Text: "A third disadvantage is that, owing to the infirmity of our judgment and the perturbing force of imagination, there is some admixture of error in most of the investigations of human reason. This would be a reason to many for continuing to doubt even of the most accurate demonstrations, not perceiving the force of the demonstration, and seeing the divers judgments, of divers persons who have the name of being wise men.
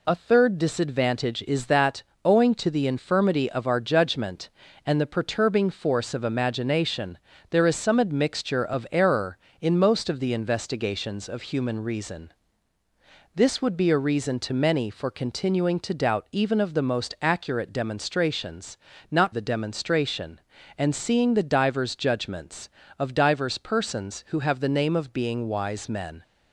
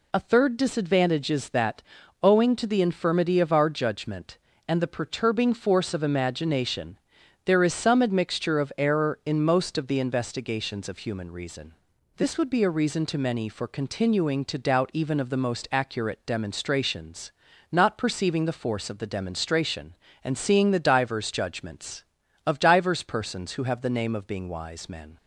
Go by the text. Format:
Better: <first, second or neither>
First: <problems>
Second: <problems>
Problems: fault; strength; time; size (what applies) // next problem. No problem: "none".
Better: second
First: skips "perceiving the force of"; at 19.3 s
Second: none